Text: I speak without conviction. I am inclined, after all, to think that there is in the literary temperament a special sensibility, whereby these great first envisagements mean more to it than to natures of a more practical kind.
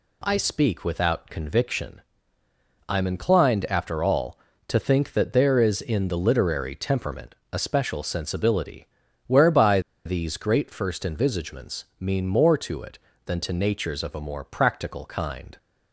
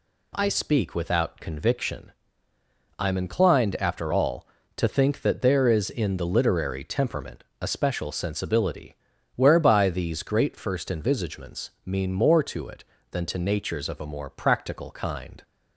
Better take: second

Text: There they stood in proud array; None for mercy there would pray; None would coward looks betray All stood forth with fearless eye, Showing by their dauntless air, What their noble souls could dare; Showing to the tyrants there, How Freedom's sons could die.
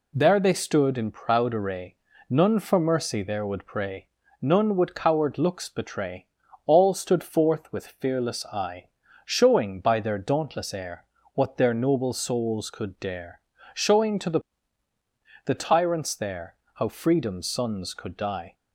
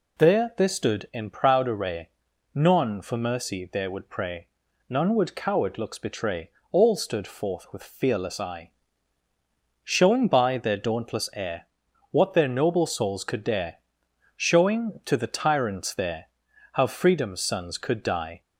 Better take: second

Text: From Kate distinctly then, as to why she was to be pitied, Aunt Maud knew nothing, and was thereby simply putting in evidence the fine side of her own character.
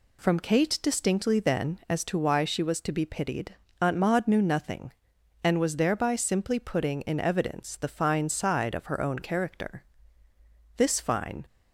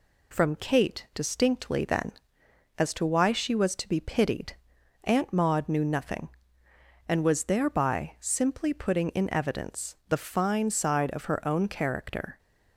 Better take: second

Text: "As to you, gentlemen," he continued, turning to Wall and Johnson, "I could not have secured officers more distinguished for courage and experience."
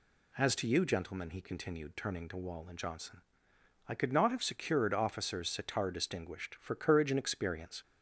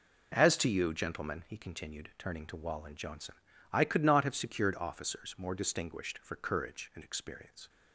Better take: second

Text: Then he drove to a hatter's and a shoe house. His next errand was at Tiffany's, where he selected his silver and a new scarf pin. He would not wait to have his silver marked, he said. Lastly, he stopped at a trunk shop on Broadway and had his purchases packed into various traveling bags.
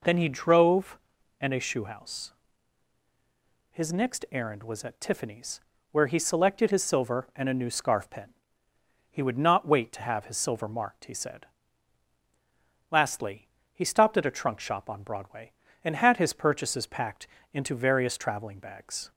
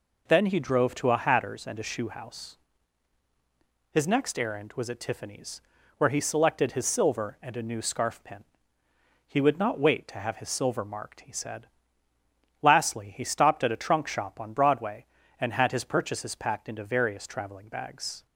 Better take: second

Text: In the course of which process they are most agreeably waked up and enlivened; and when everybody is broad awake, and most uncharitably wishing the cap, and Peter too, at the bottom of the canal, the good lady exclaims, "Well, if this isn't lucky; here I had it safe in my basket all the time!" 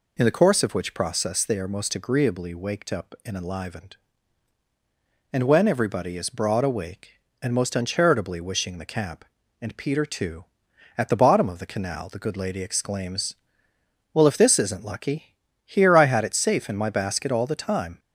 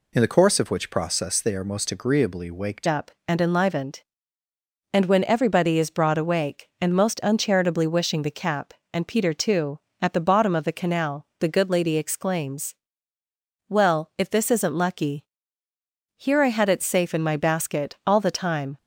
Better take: first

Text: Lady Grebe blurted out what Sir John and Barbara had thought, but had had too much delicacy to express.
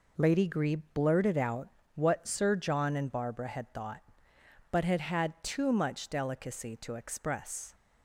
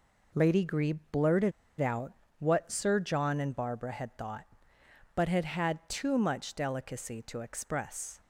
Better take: first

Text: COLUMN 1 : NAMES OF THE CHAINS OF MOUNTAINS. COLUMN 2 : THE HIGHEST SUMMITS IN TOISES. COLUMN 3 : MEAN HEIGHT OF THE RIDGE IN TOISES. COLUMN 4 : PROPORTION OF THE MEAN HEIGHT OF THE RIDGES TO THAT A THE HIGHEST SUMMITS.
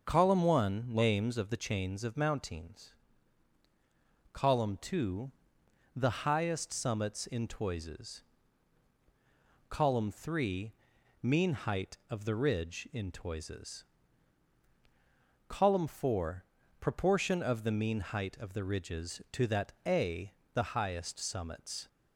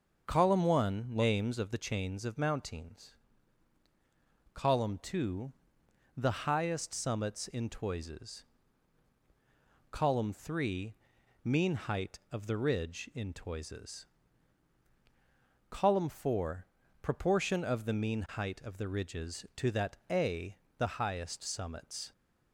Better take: neither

